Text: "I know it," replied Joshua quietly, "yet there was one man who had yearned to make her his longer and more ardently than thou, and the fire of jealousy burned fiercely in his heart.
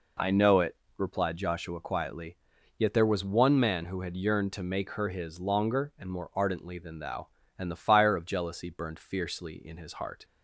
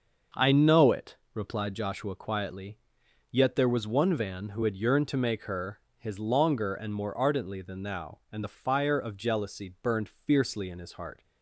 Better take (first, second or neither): first